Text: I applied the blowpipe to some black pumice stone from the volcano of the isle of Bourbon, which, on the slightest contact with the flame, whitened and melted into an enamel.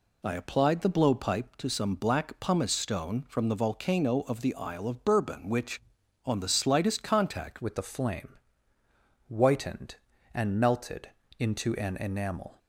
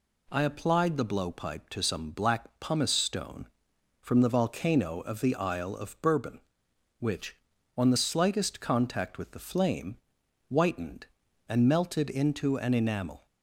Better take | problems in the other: second | changes voice at "with"; from 7.6 s on; 4.9 s long // pauses between "melted" and "into"; slight; at 11.0 s; 0.28 s long

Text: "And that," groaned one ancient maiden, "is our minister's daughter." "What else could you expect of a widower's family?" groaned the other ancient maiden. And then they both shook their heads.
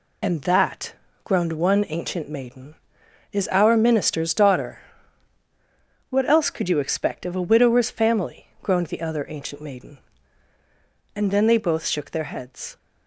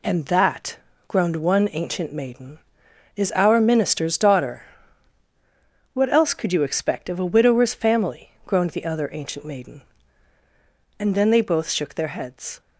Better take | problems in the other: second | loses the start of "And"; at 0.2 s; 40 ms

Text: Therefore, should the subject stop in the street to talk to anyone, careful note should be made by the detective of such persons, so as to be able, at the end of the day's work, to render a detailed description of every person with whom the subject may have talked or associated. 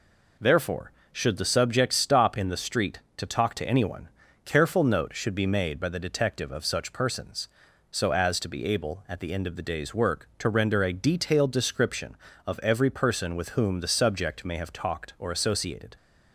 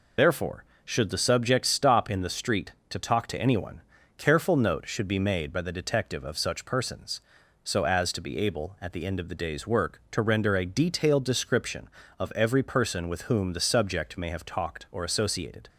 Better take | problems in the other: first | loses the start of "Therefore"; at 0.1 s; 60 ms

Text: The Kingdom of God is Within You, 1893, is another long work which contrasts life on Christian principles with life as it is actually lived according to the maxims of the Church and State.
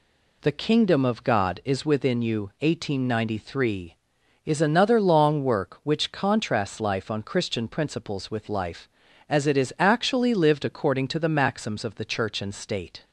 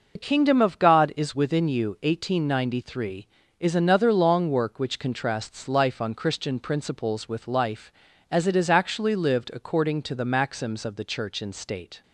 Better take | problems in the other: first | loses the start of "The"; at 0.1 s; 70 ms

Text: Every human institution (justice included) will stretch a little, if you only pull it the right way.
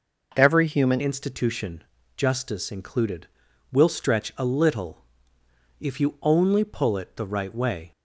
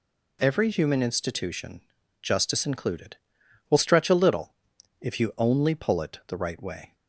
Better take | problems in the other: second | changes voice at "institution"; from 1.0 s on; 6.9 s long

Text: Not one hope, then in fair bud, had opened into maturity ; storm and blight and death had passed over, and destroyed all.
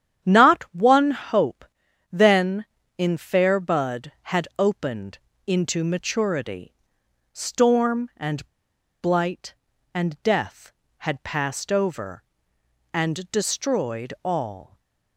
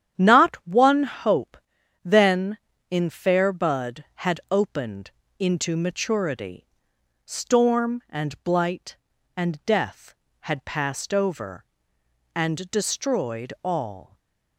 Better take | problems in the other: second | starts louder than the rest; strong; until 1.3 s; 9.5 dB; strong in the second // pauses between "opened" and "into"; slight; at 5.1 s; 0.30 s long; slight in the second // pauses between "and" and "blight"; noticeable; at 8.4 s; 0.54 s long // stays silent after the last word; slight; from 14.6 s on; 0.5 s long; slight in the second

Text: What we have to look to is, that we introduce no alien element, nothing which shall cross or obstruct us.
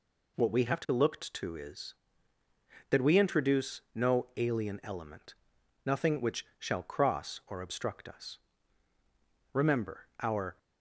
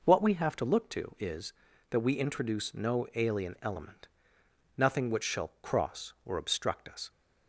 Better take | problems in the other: second | goes on to say "Remember our"; noticeable; from 9.5 s on; 1.0 s long

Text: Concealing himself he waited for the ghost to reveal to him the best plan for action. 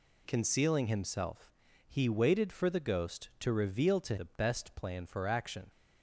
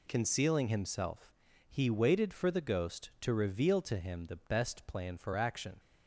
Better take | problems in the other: second | pauses between "himself" and "he"; slight; at 1.5 s; 0.36 s long; slight in the second // skips "him"; at 4.1 s

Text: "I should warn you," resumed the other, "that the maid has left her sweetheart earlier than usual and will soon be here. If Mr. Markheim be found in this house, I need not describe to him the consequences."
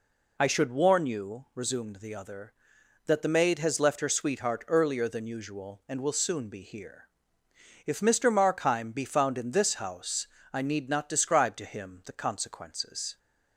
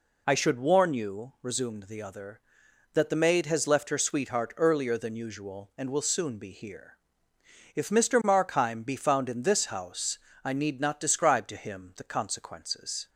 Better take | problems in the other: neither | none

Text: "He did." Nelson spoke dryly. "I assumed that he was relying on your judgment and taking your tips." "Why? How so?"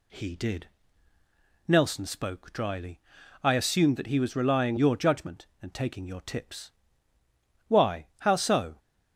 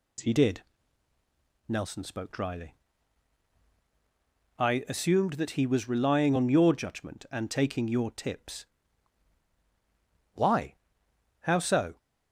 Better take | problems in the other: second | skips "on"; at 4.7 s

